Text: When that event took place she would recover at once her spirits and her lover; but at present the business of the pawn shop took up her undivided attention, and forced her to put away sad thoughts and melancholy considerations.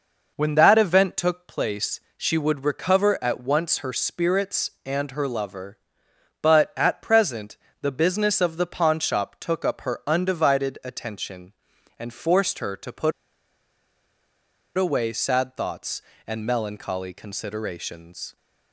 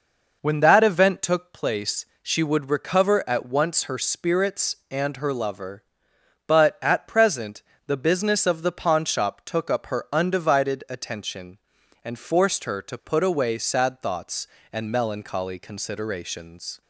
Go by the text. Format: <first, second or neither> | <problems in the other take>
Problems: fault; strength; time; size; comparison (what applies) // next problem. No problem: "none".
second | pauses between "place" and "she"; slight; at 1.9 s; 0.16 s long; slight in the second // pauses between "present" and "the"; slight; at 7.5 s; 0.26 s long; slight in the second // pauses between "put" and "away"; strong; at 13.1 s; 1.6 s long